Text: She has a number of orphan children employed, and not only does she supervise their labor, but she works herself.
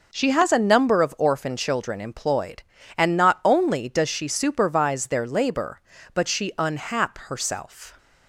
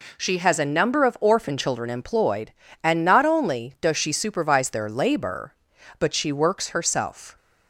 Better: second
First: says "unhap" for "works"; at 6.5 s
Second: none

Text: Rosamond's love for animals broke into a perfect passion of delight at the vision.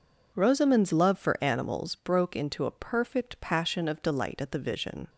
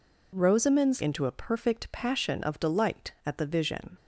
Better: first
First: none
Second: skips "love for animals broke"; at 1.0 s

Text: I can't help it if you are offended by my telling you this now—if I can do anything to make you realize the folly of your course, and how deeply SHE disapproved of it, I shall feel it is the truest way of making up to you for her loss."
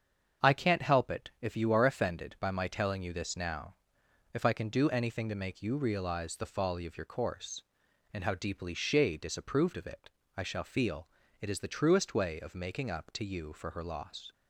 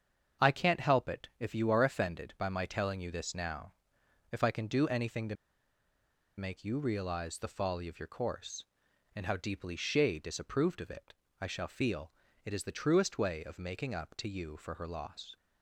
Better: first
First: starts louder than the rest; strong; until 1.5 s; 7 dB // pauses between "feel" and "it"; slight; at 11.0 s; 0.34 s long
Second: starts louder than the rest; strong; until 1.4 s; 7.5 dB // pauses between "to" and "make"; at 5.3 s; 1.0 s long // pauses between "feel" and "it"; slight; at 12.0 s; 0.34 s long

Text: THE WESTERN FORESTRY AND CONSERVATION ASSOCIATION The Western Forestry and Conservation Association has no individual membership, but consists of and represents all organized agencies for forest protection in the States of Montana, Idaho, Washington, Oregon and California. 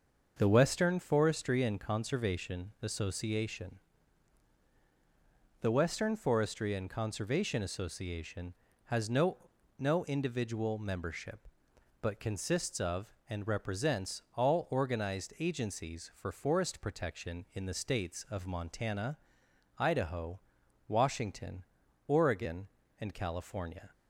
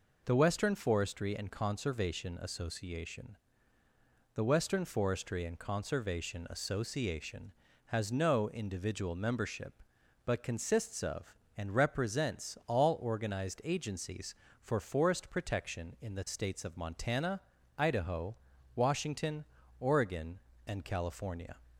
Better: second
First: starts louder than the rest; until 1.4 s; 6.5 dB // pauses between "ASSOCIATION" and "The"; strong; at 3.7 s; 1.8 s long // says "no" twice; at 9.7 s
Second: pauses between "ASSOCIATION" and "The"; at 3.3 s; 1.0 s long

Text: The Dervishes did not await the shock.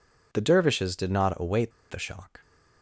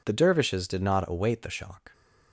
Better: second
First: pauses between "await" and "the"; slight; at 1.7 s; 0.20 s long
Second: none

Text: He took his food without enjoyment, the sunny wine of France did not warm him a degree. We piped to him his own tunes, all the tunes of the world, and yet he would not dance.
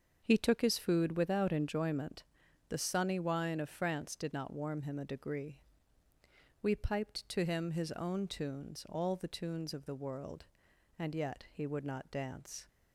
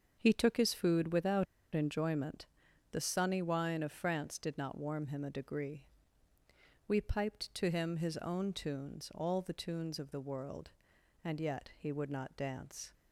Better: first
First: starts louder than the rest; until 1.2 s; 7 dB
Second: starts louder than the rest; until 1.2 s; 7 dB // pauses between "without" and "enjoyment"; slight; at 1.4 s; 0.29 s long

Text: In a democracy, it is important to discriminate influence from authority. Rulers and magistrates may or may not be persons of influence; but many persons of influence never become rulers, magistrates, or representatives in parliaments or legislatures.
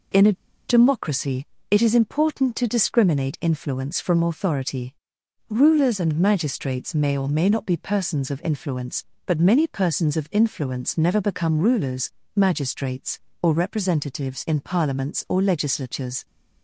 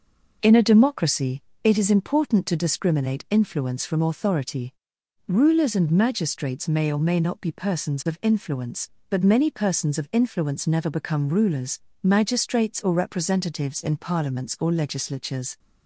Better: second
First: pauses between "a" and "democracy"; slight; at 0.3 s; 0.35 s long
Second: none

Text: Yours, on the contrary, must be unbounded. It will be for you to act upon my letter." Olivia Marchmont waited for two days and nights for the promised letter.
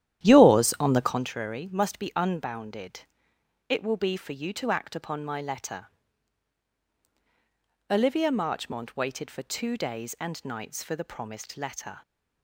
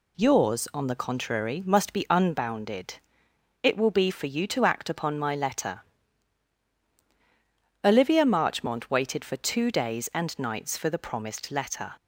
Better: second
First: starts louder than the rest; strong; until 1.3 s; 11.5 dB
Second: none

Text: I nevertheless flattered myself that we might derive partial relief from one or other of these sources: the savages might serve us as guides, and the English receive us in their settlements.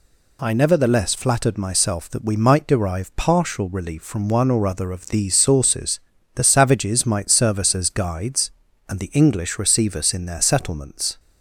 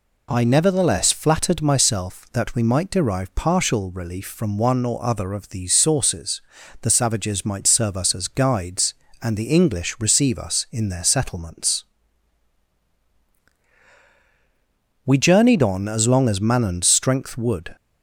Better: first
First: none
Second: goes on to say "We journeyed on as long as Manon's strength would"; strong; from 15.0 s on; 2.7 s long

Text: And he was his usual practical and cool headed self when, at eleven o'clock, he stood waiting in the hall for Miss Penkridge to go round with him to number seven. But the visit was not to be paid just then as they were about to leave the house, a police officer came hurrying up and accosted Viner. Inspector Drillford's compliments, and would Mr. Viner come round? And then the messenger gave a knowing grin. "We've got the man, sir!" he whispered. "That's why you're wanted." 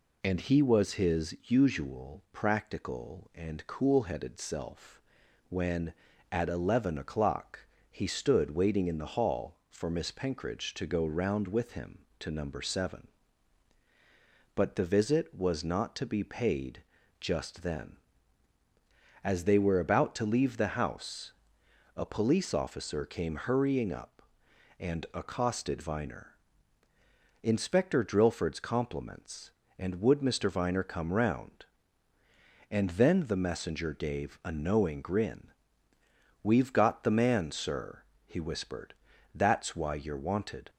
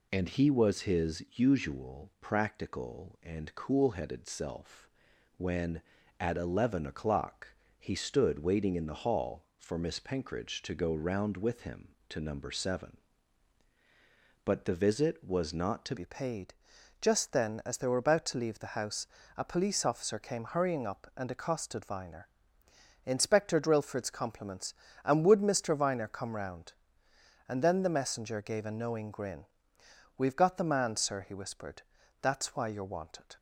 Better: first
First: pauses between "self" and "when"; noticeable; at 5.0 s; 0.48 s long // pauses between "paid" and "just"; at 16.8 s; 0.38 s long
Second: pauses between "self" and "when"; noticeable; at 4.8 s; 0.48 s long // changes voice at "be"; from 15.9 s on; 17.4 s long // pauses between "paid" and "just"; noticeable; at 16.5 s; 0.46 s long

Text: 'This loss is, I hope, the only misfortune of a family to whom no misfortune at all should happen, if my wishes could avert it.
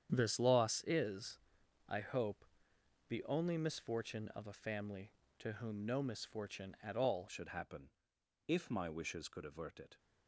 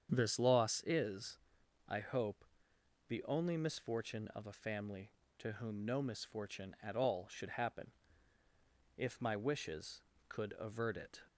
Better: second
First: starts louder than the rest; strong; until 1.1 s; 8.5 dB // changes voice at "should"; from 7.2 s on; 2.7 s long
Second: starts louder than the rest; strong; until 1.1 s; 7.5 dB

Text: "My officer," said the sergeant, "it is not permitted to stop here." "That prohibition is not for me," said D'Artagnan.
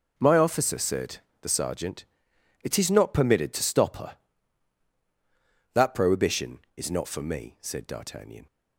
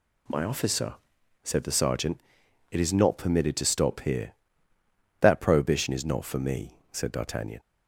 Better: second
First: pauses between "said" and "the"; slight; at 1.2 s; 0.22 s long // says "her" for "here"; at 3.9 s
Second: none

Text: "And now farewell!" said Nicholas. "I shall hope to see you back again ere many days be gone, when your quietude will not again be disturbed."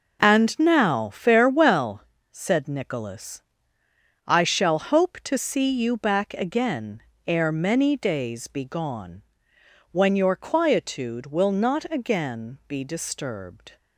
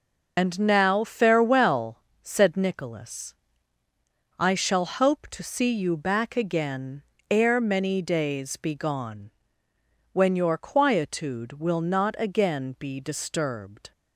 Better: first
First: pauses between "again" and "ere"; slight; at 7.0 s; 0.26 s long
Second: loses the start of "And"; at 0.3 s; 35 ms // pauses between "again" and "ere"; slight; at 7.0 s; 0.28 s long

